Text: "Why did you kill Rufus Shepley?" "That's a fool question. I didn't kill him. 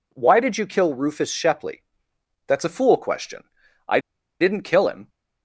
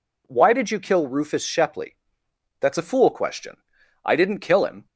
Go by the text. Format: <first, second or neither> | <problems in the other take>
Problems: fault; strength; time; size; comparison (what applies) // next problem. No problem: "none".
second | pauses between "I" and "didn't"; at 3.9 s; 0.41 s long